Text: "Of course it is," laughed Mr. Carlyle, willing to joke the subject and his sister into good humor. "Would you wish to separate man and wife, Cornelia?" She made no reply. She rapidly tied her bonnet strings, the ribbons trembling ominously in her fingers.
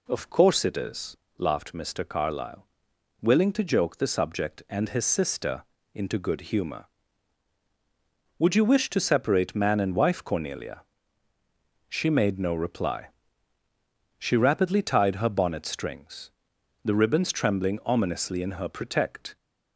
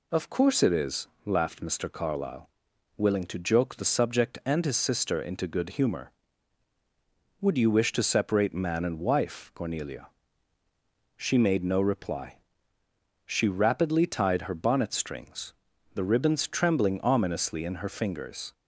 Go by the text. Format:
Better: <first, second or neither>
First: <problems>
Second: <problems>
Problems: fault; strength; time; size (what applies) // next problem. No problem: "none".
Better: second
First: pauses between "sister" and "into"; slight; at 5.6 s; 0.30 s long // says "protect" for "fingers"; at 18.6 s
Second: none